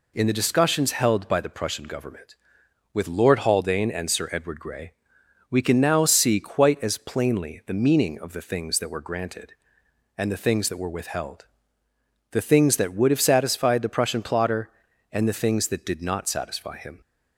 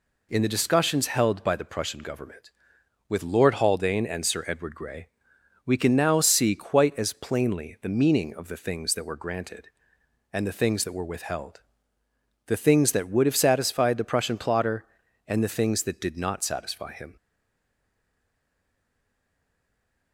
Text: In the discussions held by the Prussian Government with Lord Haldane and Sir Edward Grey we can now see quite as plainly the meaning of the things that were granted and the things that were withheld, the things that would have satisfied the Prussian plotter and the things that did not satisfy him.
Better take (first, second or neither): first